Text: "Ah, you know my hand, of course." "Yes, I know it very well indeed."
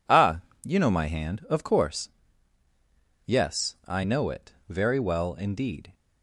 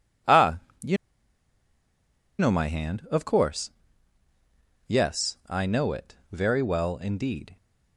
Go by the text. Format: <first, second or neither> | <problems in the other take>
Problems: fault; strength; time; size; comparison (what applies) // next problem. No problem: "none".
first | pauses between "you" and "know"; strong; at 0.9 s; 1.4 s long // pauses between "it" and "very"; slight; at 6.1 s; 0.16 s long; slight in the first